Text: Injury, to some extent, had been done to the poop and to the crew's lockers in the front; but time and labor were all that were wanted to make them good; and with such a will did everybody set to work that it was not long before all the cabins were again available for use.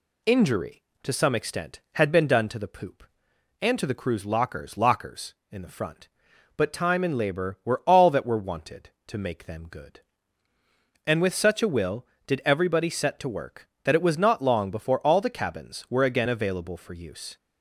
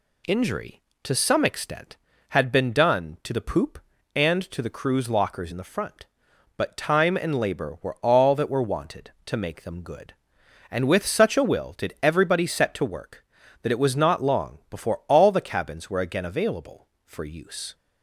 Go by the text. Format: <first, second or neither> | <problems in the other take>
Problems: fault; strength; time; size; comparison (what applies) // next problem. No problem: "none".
second | says "lockers" twice; at 4.7 s